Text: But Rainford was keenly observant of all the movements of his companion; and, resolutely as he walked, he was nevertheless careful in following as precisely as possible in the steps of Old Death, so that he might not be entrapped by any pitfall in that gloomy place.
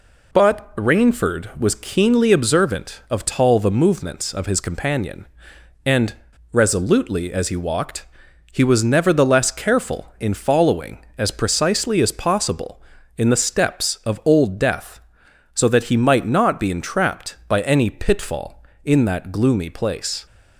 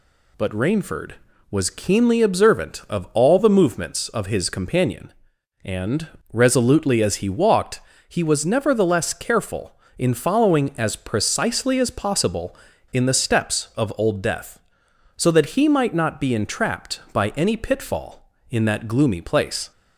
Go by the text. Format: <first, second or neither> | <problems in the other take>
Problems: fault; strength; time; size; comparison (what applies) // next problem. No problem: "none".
second | says "tall" for "all"; at 3.2 s